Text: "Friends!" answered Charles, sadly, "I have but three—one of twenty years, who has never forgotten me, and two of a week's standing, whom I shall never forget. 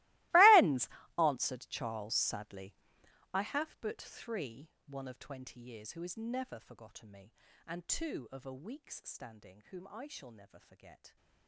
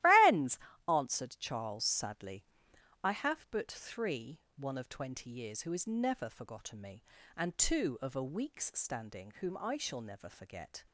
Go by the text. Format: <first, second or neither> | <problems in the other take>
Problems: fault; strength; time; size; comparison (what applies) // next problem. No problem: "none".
second | gets quieter; strong; throughout; 21 dB // starts louder than the rest; strong; until 1.6 s; 21 dB; strong in the second